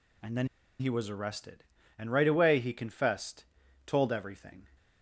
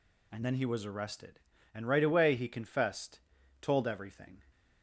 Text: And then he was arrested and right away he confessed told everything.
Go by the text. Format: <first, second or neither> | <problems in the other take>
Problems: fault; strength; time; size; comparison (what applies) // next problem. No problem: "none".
second | pauses between "then" and "he"; slight; at 0.4 s; 0.33 s long // pauses between "confessed" and "told"; at 3.4 s; 0.42 s long; also in the second